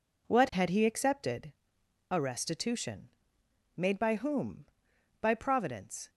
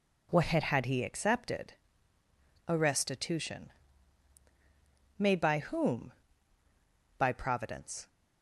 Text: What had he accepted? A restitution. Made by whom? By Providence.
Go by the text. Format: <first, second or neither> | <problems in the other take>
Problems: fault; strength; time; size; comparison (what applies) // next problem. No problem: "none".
first | says "had" twice; at 0.6 s